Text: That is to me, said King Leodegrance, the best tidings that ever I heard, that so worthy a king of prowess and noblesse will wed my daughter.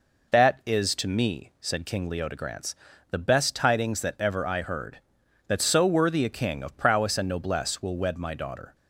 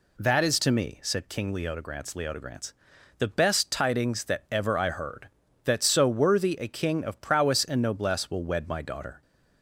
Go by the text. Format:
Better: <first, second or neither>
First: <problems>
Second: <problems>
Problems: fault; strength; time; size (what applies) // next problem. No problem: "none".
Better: first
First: none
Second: says "Leodegrance" twice; at 2.1 s